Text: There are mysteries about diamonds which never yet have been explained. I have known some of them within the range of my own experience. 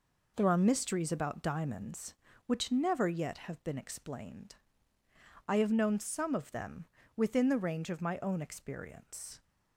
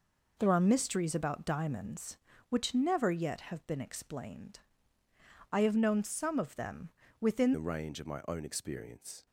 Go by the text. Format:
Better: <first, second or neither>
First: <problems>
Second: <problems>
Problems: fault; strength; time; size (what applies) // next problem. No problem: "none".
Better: first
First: pauses between "them" and "within"; slight; at 6.8 s; 0.28 s long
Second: pauses between "them" and "within"; slight; at 6.9 s; 0.28 s long // changes voice at "the"; from 7.5 s on; 1.7 s long